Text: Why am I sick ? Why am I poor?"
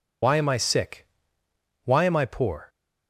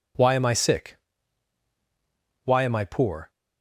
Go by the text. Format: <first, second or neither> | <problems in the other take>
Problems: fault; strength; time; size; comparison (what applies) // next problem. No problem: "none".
second | loses the start of "Why"; at 0.2 s; 60 ms